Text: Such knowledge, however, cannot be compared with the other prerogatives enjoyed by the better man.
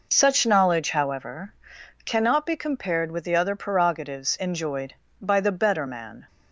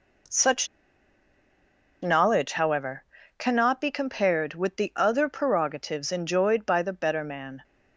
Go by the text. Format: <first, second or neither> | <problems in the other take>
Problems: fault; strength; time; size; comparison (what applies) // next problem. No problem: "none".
first | pauses between "Such" and "knowledge"; strong; at 0.6 s; 1.3 s long